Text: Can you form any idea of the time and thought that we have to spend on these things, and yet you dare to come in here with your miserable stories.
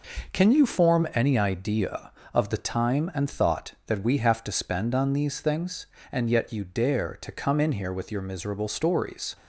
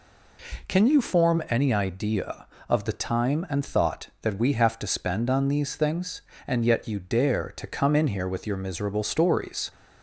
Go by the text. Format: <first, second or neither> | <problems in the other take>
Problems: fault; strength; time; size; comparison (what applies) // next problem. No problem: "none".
second | gets quieter; noticeable; throughout; 5.5 dB